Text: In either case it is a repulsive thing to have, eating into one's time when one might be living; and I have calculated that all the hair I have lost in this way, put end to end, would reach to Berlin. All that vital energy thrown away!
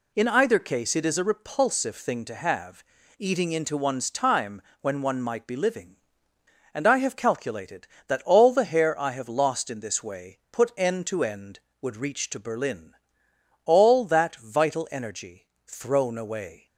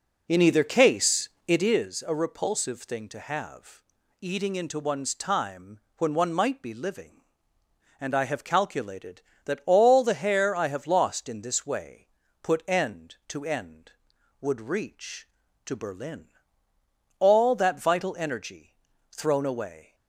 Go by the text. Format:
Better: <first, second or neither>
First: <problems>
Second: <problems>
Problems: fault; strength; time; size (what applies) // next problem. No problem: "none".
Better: first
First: pauses between "time" and "when"; slight; at 4.6 s; 0.20 s long // pauses between "energy" and "thrown"; slight; at 15.4 s; 0.18 s long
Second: starts louder than the rest; noticeable; until 1.7 s; 4.5 dB // pauses between "case" and "it"; slight; at 1.2 s; 0.18 s long // pauses between "time" and "when"; slight; at 5.8 s; 0.16 s long // pauses between "energy" and "thrown"; slight; at 18.7 s; 0.34 s long